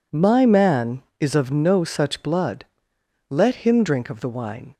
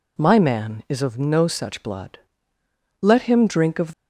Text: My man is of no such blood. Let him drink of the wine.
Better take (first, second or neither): first